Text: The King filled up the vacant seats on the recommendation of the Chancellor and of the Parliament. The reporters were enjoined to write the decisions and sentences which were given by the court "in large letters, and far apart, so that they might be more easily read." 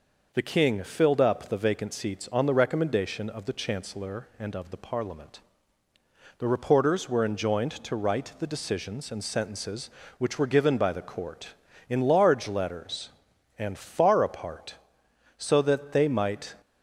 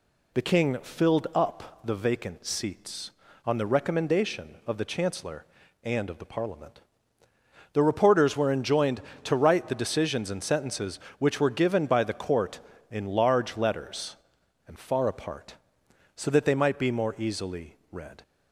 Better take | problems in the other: second | stops before "be more easily read"; at 16.6 s

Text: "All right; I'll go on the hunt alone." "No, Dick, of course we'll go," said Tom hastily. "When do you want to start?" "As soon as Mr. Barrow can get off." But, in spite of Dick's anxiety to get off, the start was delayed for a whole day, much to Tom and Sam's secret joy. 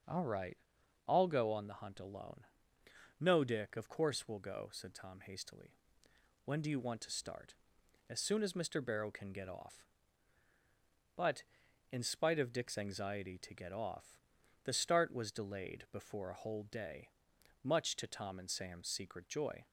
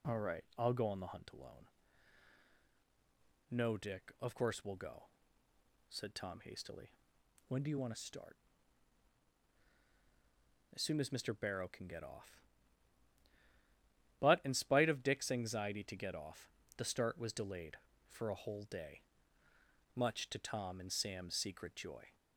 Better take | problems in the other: second | starts louder than the rest; until 1.5 s; 6.5 dB // says "before" for "for"; at 15.9 s

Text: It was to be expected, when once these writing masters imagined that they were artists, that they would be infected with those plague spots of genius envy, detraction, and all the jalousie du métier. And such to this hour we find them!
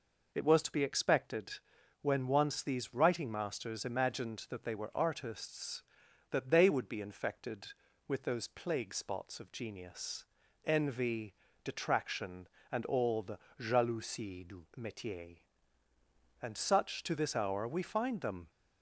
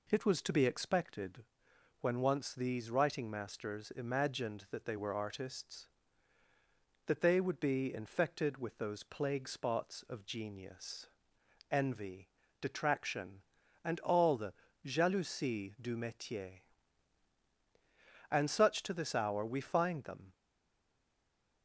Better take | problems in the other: first | pauses between "genius" and "envy"; noticeable; at 11.0 s; 0.60 s long; also in the first // pauses between "the" and "jalousie"; slight; at 14.5 s; 0.34 s long; slight in the first // stays silent after the last word; noticeable; from 20.3 s on; 1.3 s long

